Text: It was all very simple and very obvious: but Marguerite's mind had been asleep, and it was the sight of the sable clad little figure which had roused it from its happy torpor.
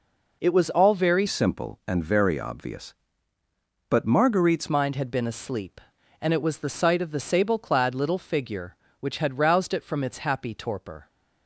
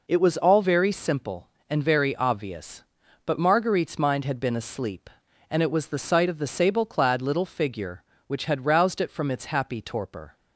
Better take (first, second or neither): second